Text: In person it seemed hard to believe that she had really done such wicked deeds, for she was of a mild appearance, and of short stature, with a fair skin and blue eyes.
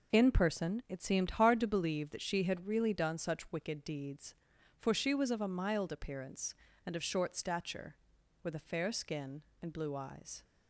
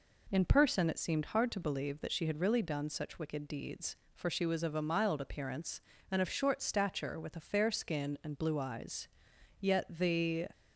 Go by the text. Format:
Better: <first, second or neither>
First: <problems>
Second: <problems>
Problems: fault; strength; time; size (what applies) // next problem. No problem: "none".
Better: first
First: none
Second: goes on to say "Yet the"; noticeable; from 9.5 s on; 0.88 s long